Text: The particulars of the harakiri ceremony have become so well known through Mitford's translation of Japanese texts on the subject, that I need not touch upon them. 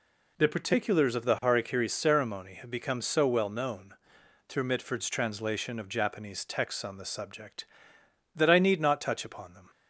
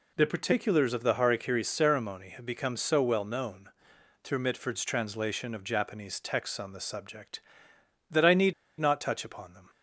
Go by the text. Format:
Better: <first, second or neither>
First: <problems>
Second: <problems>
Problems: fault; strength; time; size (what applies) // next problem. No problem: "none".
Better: first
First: pauses between "known" and "through"; noticeable; at 3.9 s; 0.54 s long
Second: pauses between "known" and "through"; noticeable; at 3.6 s; 0.54 s long // pauses between "need" and "not"; slight; at 8.5 s; 0.26 s long